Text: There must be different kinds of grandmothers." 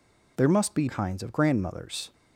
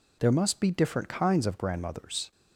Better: second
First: skips "different"; at 0.8 s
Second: none

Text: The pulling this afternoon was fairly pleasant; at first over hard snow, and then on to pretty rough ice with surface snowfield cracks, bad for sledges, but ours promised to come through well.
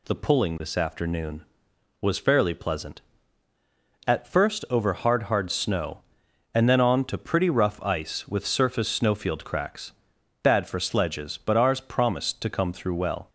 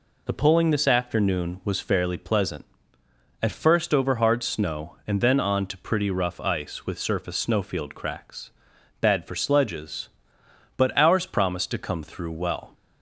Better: second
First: says "hard" twice; at 5.2 s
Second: none

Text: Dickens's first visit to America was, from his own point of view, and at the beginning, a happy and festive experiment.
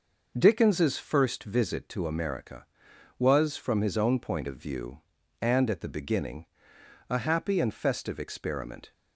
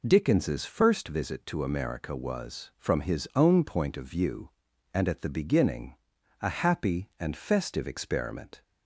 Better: neither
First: none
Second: none

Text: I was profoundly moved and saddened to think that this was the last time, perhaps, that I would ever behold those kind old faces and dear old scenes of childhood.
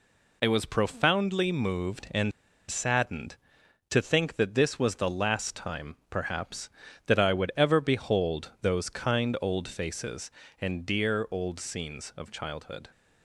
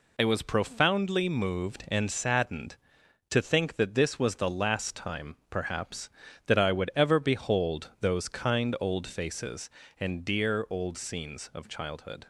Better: second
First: pauses between "and" and "saddened"; at 2.3 s; 0.39 s long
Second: none

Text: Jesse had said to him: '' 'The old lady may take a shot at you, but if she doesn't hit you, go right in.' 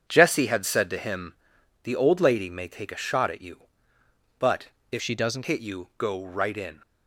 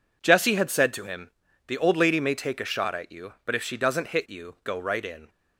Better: second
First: starts louder than the rest; strong; until 1.1 s; 8 dB // pauses between "but" and "if"; slight; at 4.6 s; 0.20 s long // changes voice from "she" to "doesn't"; from 5.0 to 5.4 s; 0.4 s long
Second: none

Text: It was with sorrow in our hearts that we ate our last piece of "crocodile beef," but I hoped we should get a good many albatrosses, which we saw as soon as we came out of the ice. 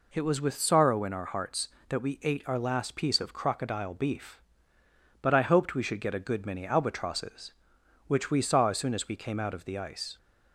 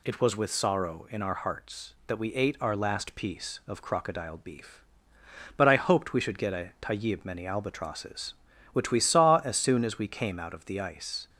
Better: first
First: none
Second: says "tayib" for "good"; at 6.8 s

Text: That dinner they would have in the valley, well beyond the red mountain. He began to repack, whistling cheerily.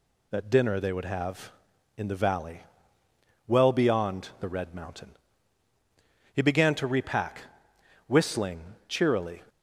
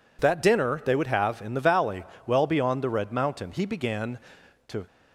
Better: first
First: none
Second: stops before "repack whistling cheerily"; at 4.8 s

